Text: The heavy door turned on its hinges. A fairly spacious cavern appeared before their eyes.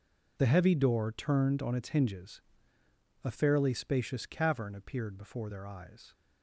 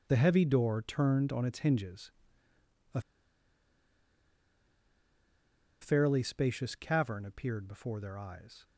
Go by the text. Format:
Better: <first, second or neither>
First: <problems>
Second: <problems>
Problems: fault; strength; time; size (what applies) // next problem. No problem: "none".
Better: first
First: none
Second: pauses between "A" and "fairly"; strong; at 3.0 s; 2.8 s long